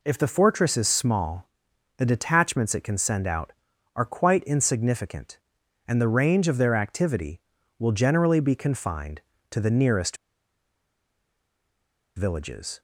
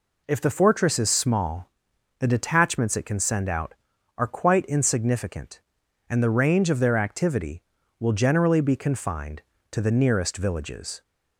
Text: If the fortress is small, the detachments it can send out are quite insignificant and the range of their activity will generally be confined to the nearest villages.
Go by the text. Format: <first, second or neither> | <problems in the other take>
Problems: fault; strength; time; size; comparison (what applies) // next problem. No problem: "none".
second | pauses between "nearest" and "villages"; strong; at 10.1 s; 2.0 s long